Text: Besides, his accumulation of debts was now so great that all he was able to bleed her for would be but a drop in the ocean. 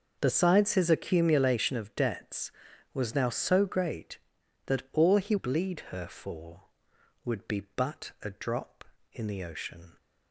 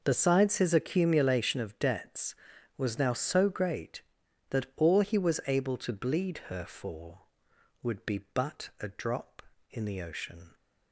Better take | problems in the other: second | skips "was able to"; at 5.3 s

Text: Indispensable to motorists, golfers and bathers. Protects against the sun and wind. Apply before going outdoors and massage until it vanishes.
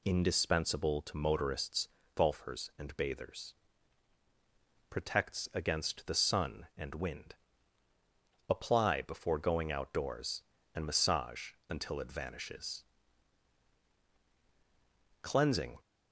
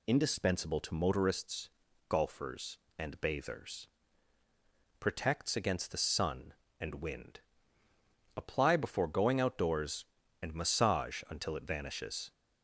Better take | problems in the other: second | pauses between "massage" and "until"; slight; at 11.5 s; 0.16 s long // goes on to say "Cleansing"; from 15.2 s on; 0.54 s long

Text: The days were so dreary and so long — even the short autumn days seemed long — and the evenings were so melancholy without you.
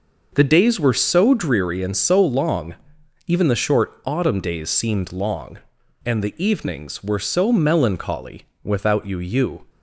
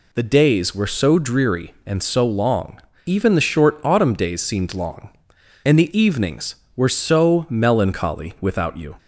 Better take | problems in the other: second | starts louder than the rest; noticeable; until 1.3 s; 6 dB // pauses between "melancholy" and "without"; slight; at 8.4 s; 0.18 s long // says "you" twice; at 9.1 s

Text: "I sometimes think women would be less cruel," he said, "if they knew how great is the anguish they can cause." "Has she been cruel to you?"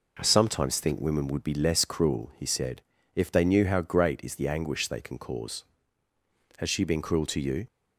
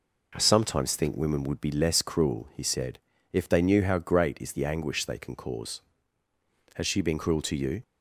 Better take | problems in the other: neither | none

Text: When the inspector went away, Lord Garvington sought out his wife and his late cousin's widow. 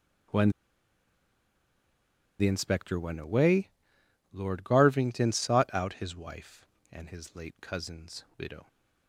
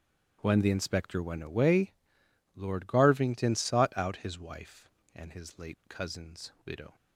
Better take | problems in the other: second | starts louder than the rest; strong; until 3.1 s; 10 dB; strong in the second // pauses between "When" and "the"; strong; at 0.5 s; 1.8 s long

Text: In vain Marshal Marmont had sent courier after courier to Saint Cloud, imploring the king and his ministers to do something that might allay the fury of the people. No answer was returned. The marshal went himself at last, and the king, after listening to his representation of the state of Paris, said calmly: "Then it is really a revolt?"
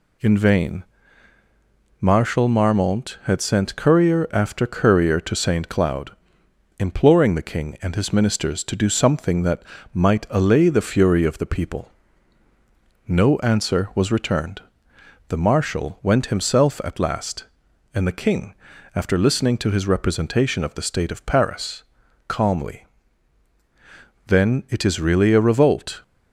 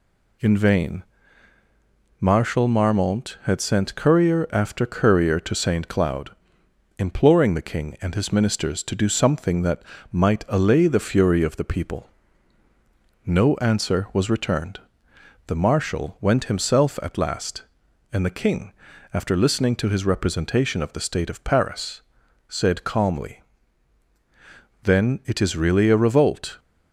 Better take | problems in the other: second | pauses between "vain" and "Marshal"; at 0.8 s; 1.1 s long; also in the second // pauses between "that" and "might"; slight; at 9.6 s; 0.30 s long; slight in the second // skips "said"; at 22.0 s

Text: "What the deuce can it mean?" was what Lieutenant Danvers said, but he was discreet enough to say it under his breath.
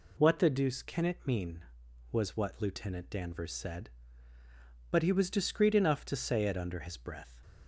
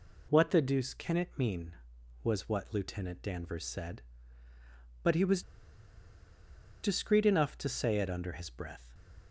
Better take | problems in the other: first | pauses between "was" and "discreet"; strong; at 5.4 s; 1.4 s long

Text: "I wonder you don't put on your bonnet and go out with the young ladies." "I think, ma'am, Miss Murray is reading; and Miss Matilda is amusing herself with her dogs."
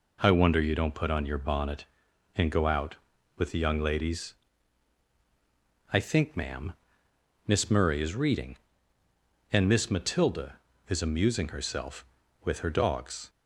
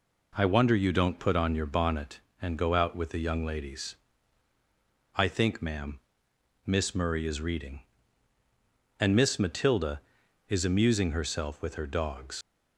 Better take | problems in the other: first | leaves "dogs" unfinished; at 12.4 s; 65 ms

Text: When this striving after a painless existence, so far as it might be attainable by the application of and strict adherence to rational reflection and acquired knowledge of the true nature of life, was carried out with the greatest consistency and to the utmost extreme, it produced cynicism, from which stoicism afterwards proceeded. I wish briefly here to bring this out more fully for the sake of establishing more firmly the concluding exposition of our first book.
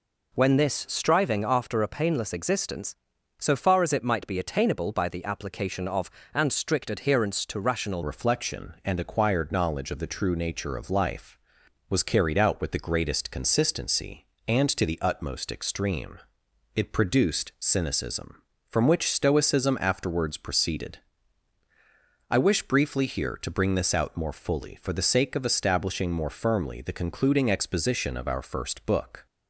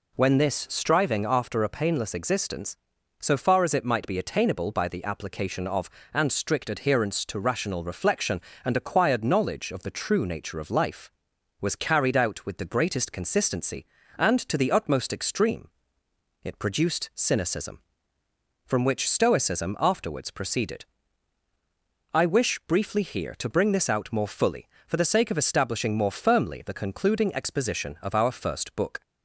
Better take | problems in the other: second | changes voice at "reflection"; from 8.0 s on; 21.2 s long

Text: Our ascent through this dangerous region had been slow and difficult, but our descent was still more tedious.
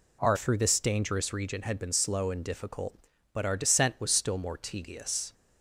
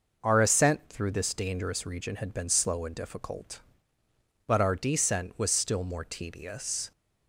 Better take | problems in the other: second | skips "ascent"; at 0.3 s

